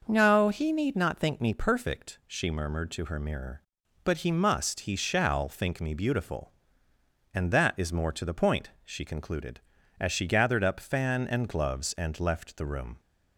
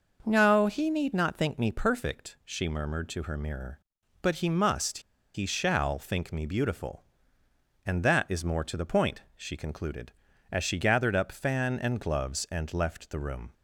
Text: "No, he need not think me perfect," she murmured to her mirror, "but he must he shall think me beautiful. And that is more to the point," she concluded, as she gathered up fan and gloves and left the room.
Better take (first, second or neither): first